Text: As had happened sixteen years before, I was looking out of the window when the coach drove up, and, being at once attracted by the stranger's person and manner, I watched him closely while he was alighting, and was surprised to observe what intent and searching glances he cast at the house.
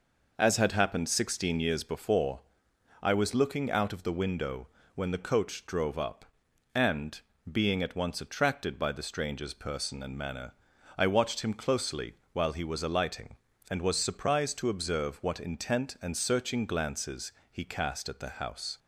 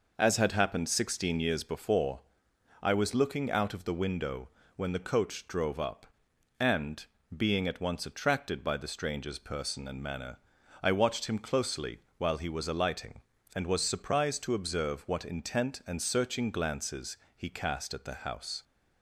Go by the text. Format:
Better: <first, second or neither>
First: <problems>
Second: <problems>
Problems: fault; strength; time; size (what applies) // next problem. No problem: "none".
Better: neither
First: pauses between "window" and "when"; slight; at 4.6 s; 0.30 s long // pauses between "closely" and "while"; slight; at 12.1 s; 0.18 s long // pauses between "glances" and "he"; slight; at 17.3 s; 0.22 s long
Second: pauses between "window" and "when"; slight; at 4.4 s; 0.30 s long // pauses between "closely" and "while"; slight; at 11.9 s; 0.18 s long // pauses between "glances" and "he"; slight; at 17.1 s; 0.22 s long